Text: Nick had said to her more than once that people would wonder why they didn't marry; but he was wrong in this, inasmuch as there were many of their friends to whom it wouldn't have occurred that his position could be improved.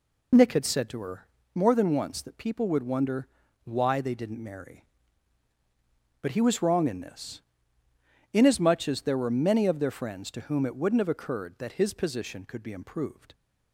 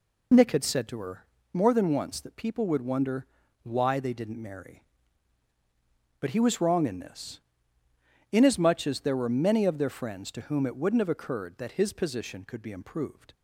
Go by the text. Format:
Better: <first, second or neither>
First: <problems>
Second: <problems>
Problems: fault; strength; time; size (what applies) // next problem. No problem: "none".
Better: neither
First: pauses between "her" and "more"; slight; at 1.2 s; 0.28 s long // pauses between "wonder" and "why"; slight; at 3.2 s; 0.36 s long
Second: pauses between "her" and "more"; slight; at 1.2 s; 0.28 s long // pauses between "wonder" and "why"; slight; at 3.2 s; 0.36 s long